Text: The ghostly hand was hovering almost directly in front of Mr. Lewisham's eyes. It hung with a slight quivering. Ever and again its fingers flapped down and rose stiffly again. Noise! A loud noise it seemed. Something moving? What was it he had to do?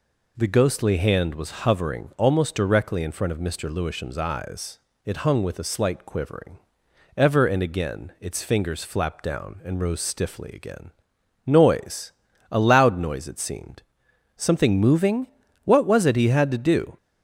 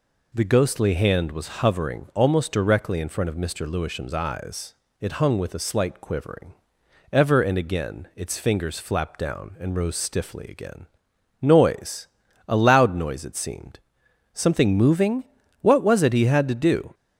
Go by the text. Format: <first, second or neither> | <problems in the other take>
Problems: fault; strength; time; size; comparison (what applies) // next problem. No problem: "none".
neither | none